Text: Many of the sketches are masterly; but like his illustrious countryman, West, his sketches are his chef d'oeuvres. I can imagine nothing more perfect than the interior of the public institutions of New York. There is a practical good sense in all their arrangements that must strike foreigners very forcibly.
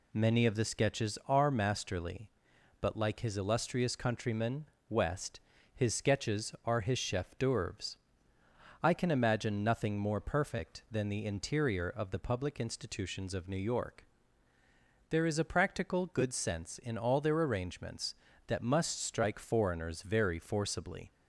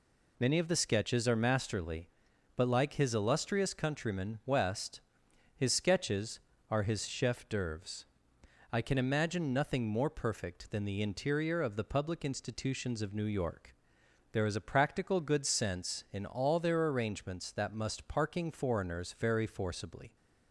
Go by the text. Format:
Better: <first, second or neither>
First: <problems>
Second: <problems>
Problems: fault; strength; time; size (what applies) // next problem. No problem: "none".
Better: first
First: none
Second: says "parking" for "strike"; at 18.0 s